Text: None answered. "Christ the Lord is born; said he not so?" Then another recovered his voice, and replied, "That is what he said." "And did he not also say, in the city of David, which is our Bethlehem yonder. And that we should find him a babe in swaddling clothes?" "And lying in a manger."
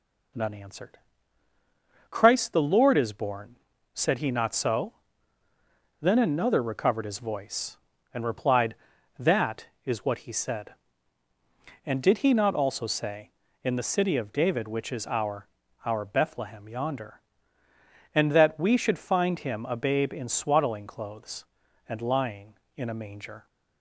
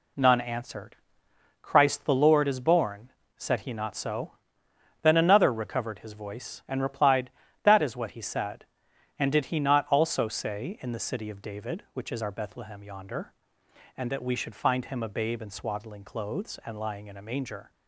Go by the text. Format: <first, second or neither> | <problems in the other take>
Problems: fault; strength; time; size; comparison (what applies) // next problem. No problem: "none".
second | says "our" twice; at 15.8 s